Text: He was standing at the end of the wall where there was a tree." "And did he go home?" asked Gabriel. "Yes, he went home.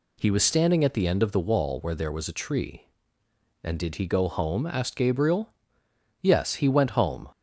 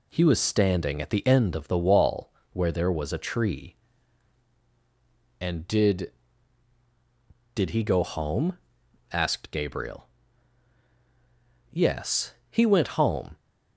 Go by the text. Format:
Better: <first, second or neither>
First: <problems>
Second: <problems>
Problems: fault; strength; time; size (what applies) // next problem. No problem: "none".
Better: first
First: none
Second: pauses between "wall" and "where"; slight; at 2.3 s; 0.20 s long // says "did" twice; at 7.5 s